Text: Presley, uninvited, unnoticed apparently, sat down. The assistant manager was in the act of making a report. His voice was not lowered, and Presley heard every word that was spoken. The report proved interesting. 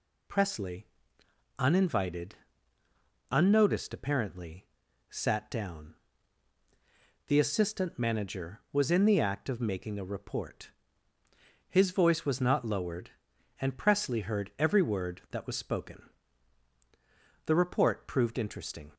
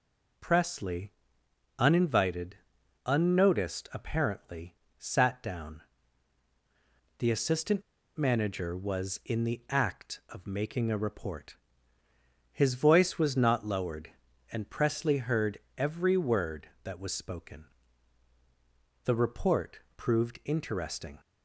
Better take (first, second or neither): first